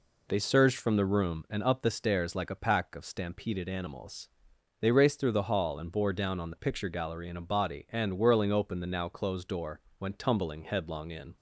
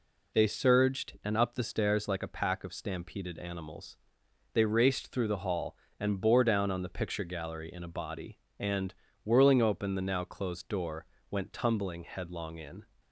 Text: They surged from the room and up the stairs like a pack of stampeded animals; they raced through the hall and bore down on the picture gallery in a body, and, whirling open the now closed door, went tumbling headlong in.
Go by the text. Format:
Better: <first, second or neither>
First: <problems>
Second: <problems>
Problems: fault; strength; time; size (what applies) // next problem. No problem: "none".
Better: first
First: none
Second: skips "from the room"; at 1.2 s